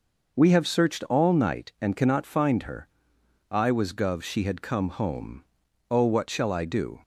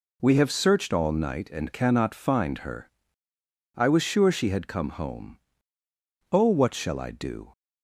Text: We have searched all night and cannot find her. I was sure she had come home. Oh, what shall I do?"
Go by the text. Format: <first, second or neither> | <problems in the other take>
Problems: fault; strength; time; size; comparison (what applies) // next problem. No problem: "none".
second | says "gov" for "sure"; at 3.9 s